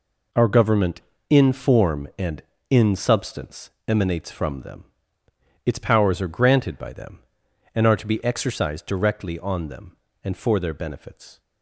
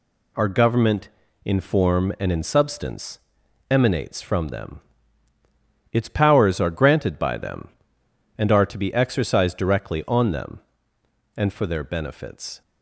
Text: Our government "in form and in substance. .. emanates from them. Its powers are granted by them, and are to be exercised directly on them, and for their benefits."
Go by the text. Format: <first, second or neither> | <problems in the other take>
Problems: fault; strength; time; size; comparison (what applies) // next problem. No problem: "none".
neither | none